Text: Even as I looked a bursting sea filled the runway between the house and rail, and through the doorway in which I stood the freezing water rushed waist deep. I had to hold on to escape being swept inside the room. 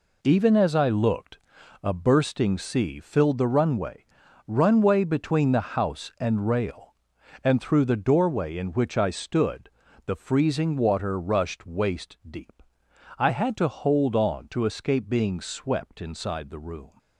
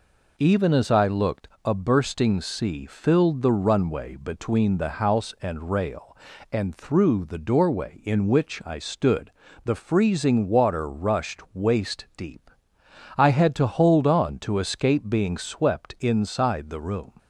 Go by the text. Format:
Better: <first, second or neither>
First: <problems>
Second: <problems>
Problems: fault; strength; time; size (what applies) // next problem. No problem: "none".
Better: second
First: pauses between "looked" and "a"; at 1.3 s; 0.44 s long // says "runway" twice; at 4.4 s // pauses between "stood" and "the"; slight; at 9.7 s; 0.34 s long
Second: pauses between "looked" and "a"; slight; at 1.4 s; 0.18 s long // pauses between "stood" and "the"; slight; at 9.3 s; 0.34 s long